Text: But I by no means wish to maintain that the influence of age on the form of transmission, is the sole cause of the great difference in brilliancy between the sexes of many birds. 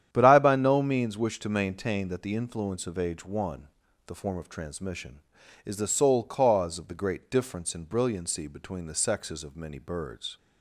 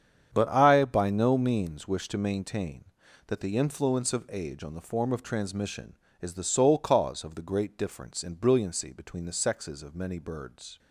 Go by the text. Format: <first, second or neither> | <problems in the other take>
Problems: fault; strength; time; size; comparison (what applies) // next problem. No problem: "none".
second | starts louder than the rest; strong; until 1.1 s; 10 dB; strong in the second // says "one" for "on"; at 3.2 s